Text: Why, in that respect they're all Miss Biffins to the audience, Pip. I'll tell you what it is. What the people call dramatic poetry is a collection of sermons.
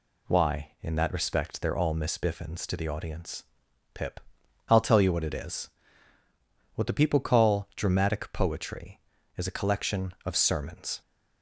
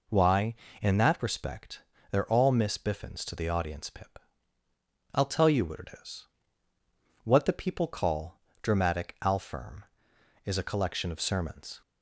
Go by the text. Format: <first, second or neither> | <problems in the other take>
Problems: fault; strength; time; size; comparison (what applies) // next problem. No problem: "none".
first | pauses between "respect" and "they're"; slight; at 1.8 s; 0.30 s long // pauses between "call" and "dramatic"; slight; at 8.3 s; 0.22 s long // says "alfirm" for "poetry"; at 9.2 s